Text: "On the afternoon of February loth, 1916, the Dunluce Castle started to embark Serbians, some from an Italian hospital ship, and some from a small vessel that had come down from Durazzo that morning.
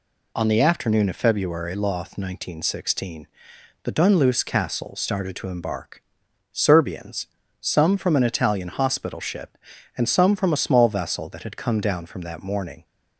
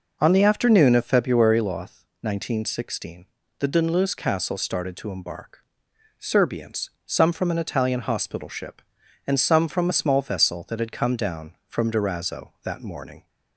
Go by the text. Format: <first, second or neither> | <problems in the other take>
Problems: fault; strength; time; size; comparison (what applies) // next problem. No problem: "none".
second | pauses between "embark" and "Serbians"; noticeable; at 6.0 s; 0.47 s long; noticeable in the second // skips "Durazzo"; at 12.2 s